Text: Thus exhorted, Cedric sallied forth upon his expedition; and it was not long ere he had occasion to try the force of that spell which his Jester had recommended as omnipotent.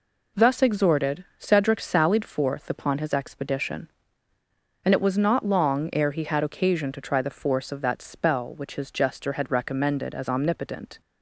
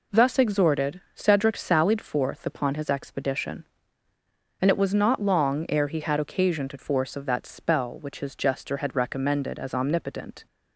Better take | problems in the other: first | skips "try the"; at 6.7 s

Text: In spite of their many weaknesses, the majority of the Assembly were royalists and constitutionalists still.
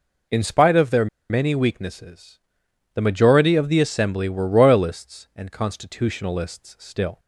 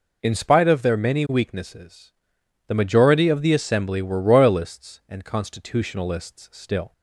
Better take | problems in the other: second | pauses between "their" and "many"; slight; at 1.0 s; 0.23 s long

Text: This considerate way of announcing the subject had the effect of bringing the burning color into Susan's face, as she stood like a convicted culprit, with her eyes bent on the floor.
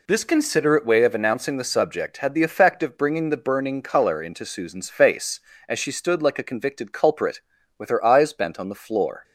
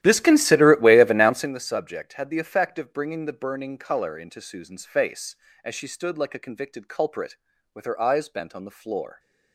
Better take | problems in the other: first | starts louder than the rest; strong; until 1.6 s; 13 dB

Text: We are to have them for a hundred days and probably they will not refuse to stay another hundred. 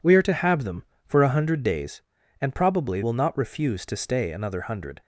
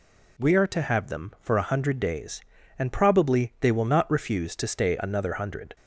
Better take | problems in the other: second | skips "they"; at 3.0 s

